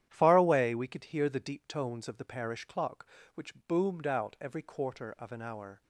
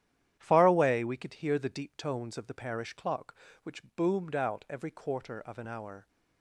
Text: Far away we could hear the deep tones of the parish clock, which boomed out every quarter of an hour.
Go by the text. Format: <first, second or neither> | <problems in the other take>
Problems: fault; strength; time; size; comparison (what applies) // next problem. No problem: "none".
neither | starts louder than the rest; strong; the same in both // pauses between "which" and "boomed"; slight; the same in both